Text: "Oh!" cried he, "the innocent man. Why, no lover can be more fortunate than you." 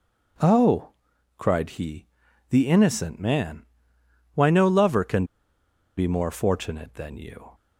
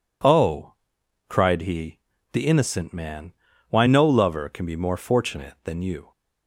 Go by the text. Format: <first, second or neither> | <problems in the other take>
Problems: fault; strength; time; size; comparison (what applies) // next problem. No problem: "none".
second | pauses between "can" and "be"; noticeable; at 5.2 s; 0.73 s long